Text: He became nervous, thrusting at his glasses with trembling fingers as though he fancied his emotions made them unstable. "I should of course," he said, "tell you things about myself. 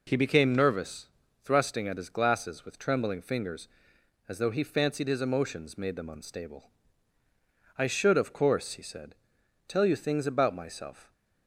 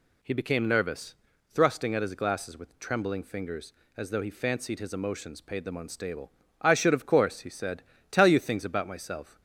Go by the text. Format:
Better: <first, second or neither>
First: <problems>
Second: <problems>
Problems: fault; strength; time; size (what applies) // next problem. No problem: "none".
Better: first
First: none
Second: says "paid" for "made"; at 5.4 s